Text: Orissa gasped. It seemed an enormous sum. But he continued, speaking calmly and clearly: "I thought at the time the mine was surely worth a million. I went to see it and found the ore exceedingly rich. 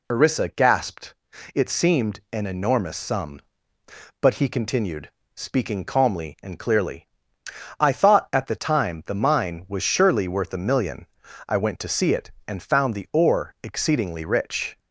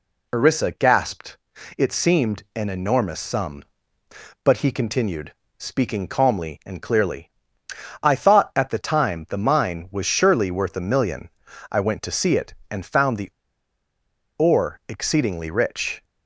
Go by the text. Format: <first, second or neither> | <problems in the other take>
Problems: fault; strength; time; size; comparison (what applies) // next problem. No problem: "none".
first | pauses between "the" and "ore"; at 13.3 s; 1.0 s long